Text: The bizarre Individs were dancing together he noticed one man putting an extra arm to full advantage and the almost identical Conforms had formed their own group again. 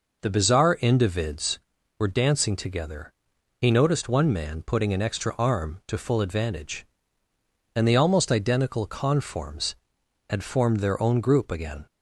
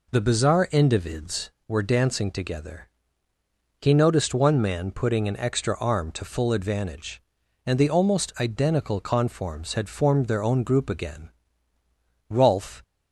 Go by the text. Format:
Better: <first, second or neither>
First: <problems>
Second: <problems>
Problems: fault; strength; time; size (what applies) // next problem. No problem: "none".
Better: first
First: pauses between "together" and "he"; noticeable; at 3.1 s; 0.46 s long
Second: pauses between "together" and "he"; noticeable; at 2.8 s; 0.92 s long // goes on to say "Rolf"; from 12.3 s on; 0.52 s long